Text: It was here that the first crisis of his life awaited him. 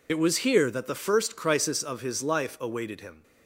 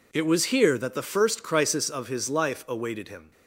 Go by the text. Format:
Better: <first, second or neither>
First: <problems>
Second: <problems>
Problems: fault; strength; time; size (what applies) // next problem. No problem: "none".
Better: second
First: loses the start of "It"; at 0.0 s; 40 ms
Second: none